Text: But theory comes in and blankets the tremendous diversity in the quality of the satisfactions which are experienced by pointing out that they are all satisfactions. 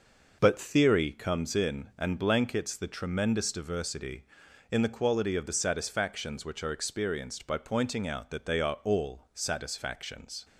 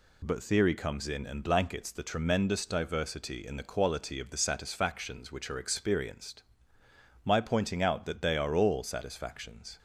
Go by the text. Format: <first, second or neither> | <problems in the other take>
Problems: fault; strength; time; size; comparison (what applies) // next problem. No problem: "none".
first | says "my" for "by"; at 7.2 s